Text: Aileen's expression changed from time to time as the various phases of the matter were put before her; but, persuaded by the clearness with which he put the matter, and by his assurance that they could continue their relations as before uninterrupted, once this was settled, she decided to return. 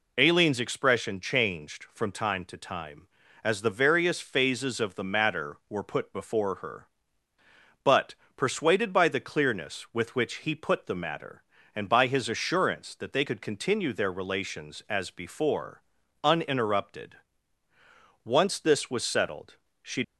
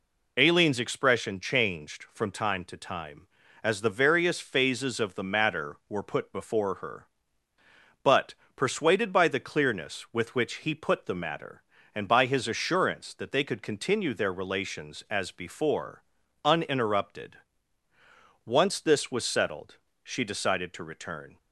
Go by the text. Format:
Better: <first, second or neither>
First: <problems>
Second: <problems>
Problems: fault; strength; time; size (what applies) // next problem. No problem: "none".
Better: second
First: pauses between "before" and "uninterrupted"; at 15.8 s; 0.44 s long // stops before "decided to return"; at 20.0 s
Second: pauses between "before" and "uninterrupted"; at 16.0 s; 0.44 s long